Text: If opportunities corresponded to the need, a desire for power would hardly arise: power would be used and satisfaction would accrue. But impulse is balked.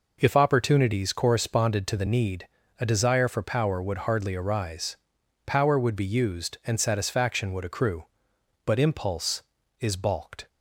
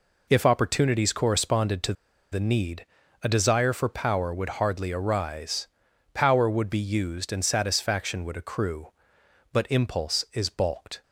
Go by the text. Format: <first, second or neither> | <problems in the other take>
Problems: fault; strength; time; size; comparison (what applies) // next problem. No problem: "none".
first | pauses between "to" and "the"; at 1.9 s; 0.38 s long